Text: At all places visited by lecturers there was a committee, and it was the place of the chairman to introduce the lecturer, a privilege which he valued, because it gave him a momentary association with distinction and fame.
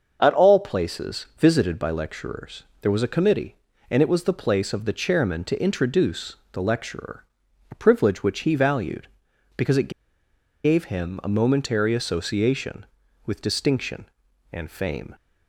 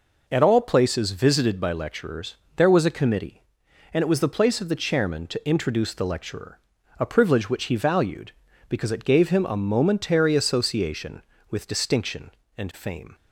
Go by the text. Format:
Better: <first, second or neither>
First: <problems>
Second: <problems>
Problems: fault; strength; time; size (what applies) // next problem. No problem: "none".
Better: second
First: starts louder than the rest; until 1.2 s; 6.5 dB // pauses between "lecturers" and "there"; slight; at 2.6 s; 0.20 s long // pauses between "introduce" and "the"; slight; at 6.3 s; 0.18 s long // pauses between "it" and "gave"; noticeable; at 9.9 s; 0.74 s long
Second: pauses between "lecturers" and "there"; slight; at 2.3 s; 0.22 s long